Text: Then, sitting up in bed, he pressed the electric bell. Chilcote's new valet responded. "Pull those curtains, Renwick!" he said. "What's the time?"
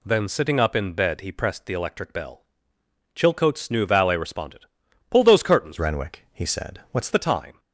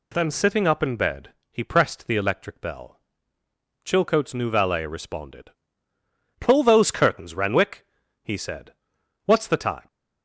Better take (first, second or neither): second